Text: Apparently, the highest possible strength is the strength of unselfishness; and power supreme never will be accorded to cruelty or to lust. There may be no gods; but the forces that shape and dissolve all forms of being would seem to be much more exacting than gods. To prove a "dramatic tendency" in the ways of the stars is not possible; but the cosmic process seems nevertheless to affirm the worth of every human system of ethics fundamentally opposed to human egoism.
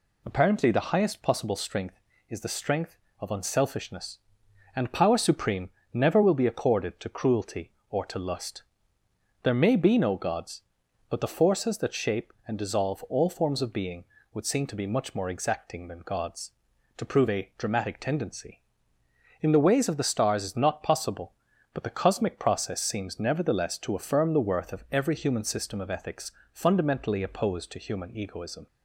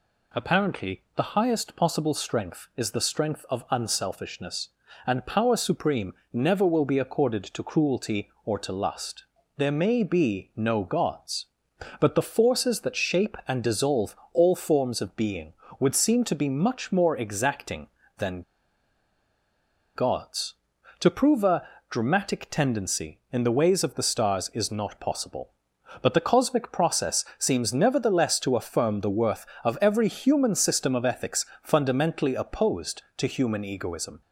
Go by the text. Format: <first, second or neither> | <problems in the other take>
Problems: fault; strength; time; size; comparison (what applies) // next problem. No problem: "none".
first | pauses between "supreme" and "never"; slight; at 6.1 s; 0.18 s long; slight in the first // pauses between "dissolve" and "all"; slight; at 14.1 s; 0.16 s long // pauses between "than" and "gods"; strong; at 18.4 s; 1.5 s long // pauses between "a" and "dramatic"; slight; at 21.6 s; 0.22 s long // pauses between "ethics" and "fundamentally"; slight; at 31.4 s; 0.18 s long; slight in the first